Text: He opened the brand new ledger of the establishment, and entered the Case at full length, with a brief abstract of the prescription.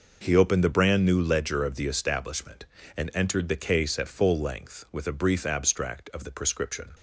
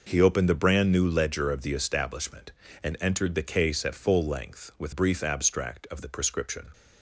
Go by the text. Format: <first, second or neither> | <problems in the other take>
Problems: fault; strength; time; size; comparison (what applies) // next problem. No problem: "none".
first | skips "a"; at 4.9 s